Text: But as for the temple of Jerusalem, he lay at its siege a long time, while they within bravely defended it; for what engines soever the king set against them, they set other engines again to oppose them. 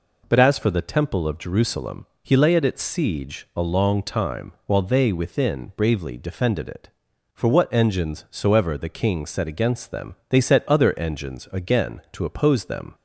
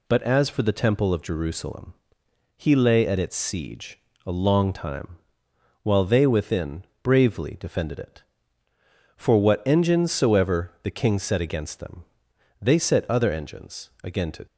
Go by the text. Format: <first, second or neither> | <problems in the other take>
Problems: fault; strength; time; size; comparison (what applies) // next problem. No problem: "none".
first | pauses between "siege" and "a"; slight; at 3.9 s; 0.26 s long // pauses between "within" and "bravely"; slight; at 6.8 s; 0.18 s long // pauses between "engines" and "again"; slight; at 13.8 s; 0.16 s long // stops before "oppose them"; at 14.4 s